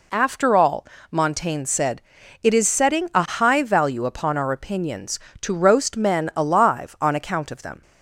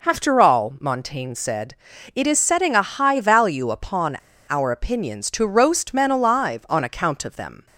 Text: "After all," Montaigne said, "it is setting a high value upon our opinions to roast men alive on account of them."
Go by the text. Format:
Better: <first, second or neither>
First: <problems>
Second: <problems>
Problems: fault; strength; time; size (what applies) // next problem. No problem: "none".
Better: first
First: none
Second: pauses between "upon" and "our"; slight; at 4.1 s; 0.28 s long